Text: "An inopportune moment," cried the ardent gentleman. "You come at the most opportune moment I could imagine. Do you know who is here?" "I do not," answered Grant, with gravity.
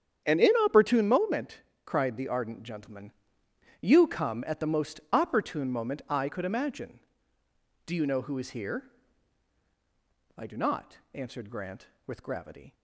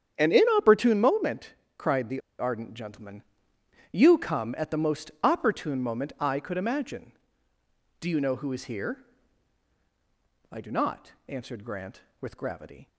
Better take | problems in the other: first | starts louder than the rest; strong; until 1.1 s; 8.5 dB; strong in the first // pauses between "the" and "ardent"; slight; at 2.2 s; 0.19 s long

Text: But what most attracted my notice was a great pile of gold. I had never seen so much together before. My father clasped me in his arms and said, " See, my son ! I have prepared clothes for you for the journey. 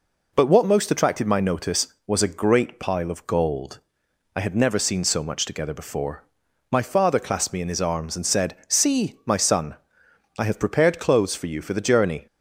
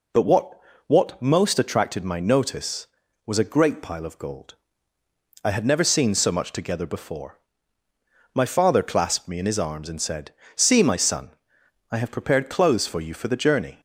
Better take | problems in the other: first | says "what" twice; at 0.8 s

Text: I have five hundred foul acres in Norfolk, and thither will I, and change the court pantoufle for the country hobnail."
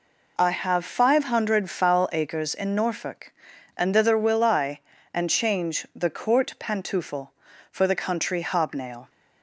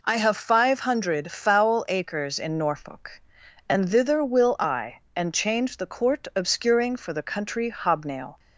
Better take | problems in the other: first | says "obscuring" for "pantoufle"; at 6.3 s

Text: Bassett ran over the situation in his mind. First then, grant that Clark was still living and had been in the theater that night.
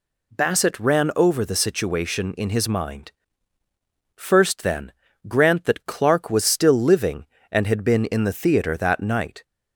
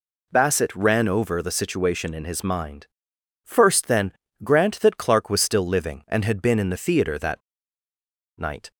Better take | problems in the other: first | pauses between "that" and "night"; noticeable; at 7.4 s; 0.97 s long

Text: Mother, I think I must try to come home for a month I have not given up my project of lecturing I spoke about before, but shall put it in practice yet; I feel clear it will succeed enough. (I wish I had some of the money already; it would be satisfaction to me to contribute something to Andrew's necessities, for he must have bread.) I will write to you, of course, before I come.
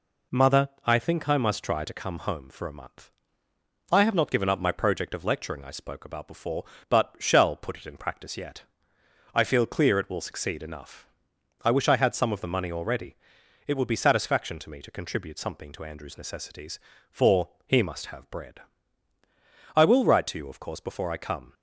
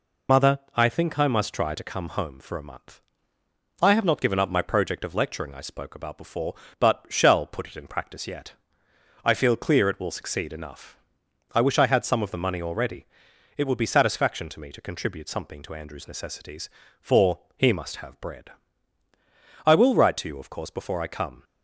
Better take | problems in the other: first | loses the start of "Mother"; at 0.2 s; 80 ms // pauses between "month" and "I"; noticeable; at 2.9 s; 0.82 s long; noticeable in the first // pauses between "for" and "he"; slight; at 17.3 s; 0.16 s long; slight in the first

